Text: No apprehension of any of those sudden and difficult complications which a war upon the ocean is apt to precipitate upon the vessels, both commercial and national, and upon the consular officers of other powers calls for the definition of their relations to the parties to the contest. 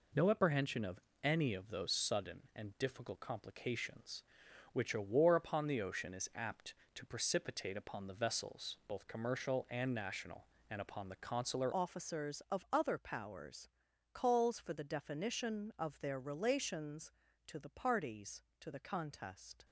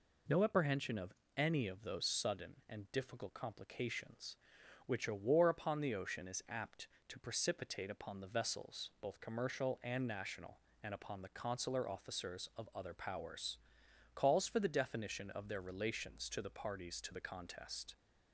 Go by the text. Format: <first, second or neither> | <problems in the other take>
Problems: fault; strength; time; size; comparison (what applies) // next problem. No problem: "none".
second | pauses between "of" and "any"; slight; at 0.9 s; 0.24 s long; slight in the second // changes voice at "officers"; from 11.7 s on; 7.9 s long // pauses between "powers" and "calls"; noticeable; at 13.6 s; 0.46 s long; noticeable in the second